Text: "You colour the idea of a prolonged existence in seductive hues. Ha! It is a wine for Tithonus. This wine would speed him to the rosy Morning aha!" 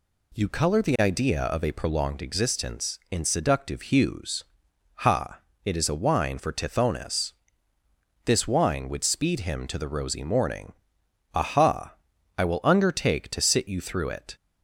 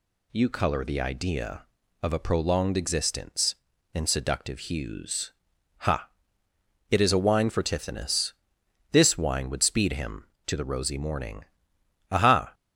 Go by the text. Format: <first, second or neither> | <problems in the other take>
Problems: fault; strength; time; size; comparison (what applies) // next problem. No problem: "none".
second | pauses between "Morning" and "aha"; noticeable; at 10.7 s; 0.60 s long; noticeable in the second // goes on to say "I will undertake to sit you through it"; strong; from 12.3 s on; 1.9 s long